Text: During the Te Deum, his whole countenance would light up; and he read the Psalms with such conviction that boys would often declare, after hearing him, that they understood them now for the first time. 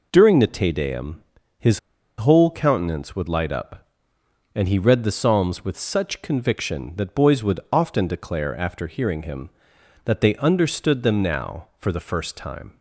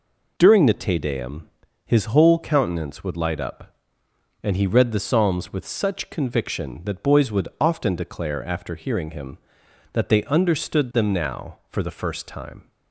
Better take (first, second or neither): second